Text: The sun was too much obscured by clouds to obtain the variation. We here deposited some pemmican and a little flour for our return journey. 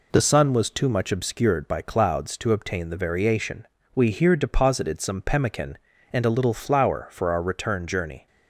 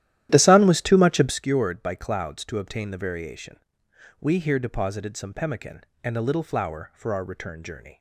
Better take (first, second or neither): first